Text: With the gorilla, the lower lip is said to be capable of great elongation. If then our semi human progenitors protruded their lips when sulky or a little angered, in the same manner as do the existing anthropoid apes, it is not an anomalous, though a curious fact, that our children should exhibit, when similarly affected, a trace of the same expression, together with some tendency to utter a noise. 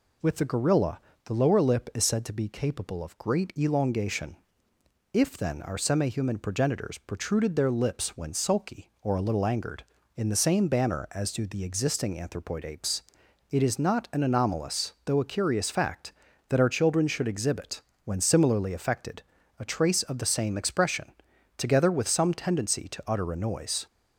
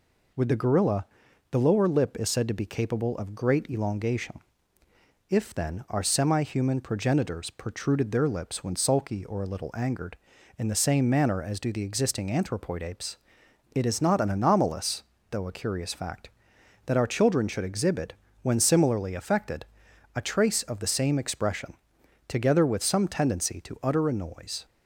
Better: second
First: says "banner" for "manner"; at 10.6 s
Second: none

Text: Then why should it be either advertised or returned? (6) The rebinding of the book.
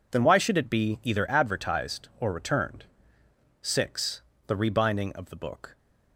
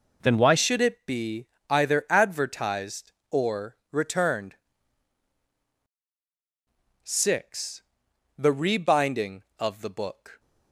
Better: first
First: none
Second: changes voice at "should"; from 0.5 s on; 9.8 s long // pauses between "be" and "either"; slight; at 1.4 s; 0.22 s long

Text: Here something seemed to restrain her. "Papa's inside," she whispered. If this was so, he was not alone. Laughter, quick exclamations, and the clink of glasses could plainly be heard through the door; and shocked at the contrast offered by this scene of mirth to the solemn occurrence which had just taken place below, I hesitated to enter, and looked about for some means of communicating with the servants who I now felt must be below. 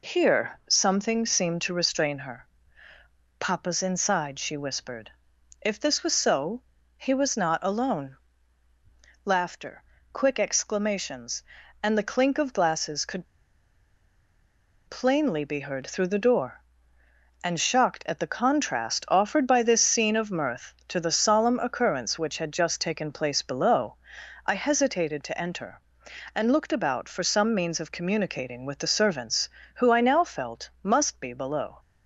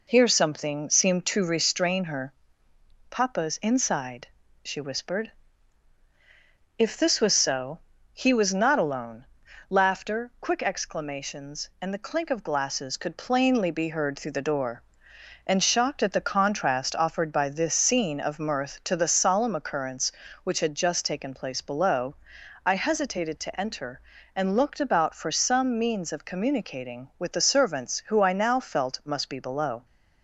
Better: second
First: pauses between "could" and "plainly"; strong; at 13.2 s; 1.6 s long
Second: none

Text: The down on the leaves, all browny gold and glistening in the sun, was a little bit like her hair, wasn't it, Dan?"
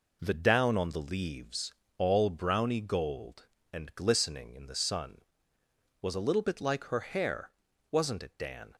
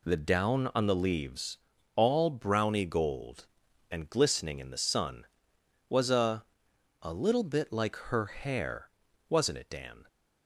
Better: first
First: none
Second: says "a" twice; at 7.0 s

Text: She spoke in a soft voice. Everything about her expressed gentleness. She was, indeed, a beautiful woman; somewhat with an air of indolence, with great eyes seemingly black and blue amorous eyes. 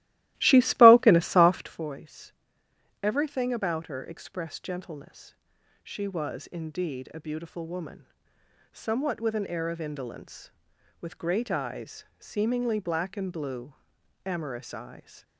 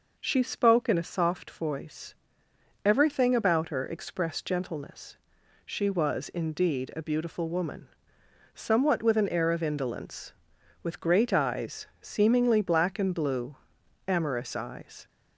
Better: second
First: starts louder than the rest; strong; until 1.9 s; 16 dB // pauses between "eyes" and "seemingly"; slight; at 12.0 s; 0.16 s long // pauses between "blue" and "amorous"; noticeable; at 13.7 s; 0.50 s long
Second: pauses between "eyes" and "seemingly"; slight; at 11.8 s; 0.16 s long // pauses between "blue" and "amorous"; noticeable; at 13.5 s; 0.50 s long

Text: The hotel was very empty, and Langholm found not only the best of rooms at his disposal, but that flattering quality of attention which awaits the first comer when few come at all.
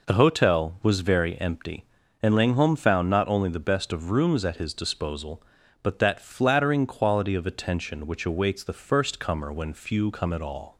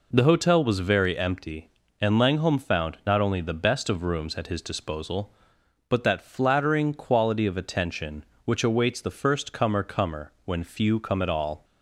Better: first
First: none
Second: says "comer" twice; at 9.8 s

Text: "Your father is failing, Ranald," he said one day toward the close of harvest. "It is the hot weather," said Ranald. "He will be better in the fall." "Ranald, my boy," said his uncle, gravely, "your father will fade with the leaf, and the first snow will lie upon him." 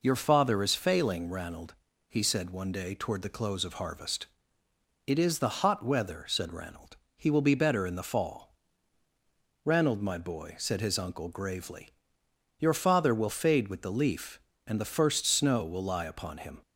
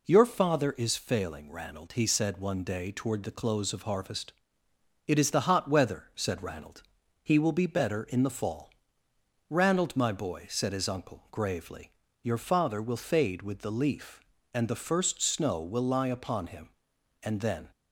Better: first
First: none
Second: goes on to say "And then"; slight; from 17.2 s on; 0.48 s long

